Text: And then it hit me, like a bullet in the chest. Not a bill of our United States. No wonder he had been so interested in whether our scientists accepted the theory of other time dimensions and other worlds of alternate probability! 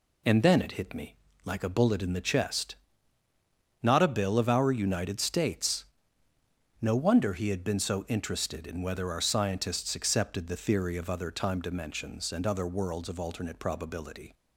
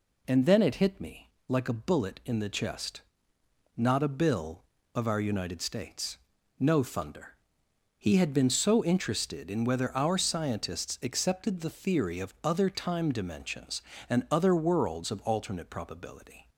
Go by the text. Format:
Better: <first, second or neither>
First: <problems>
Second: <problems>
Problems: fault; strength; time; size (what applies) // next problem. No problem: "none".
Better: first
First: none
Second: says "thunder" for "wonder"; at 6.8 s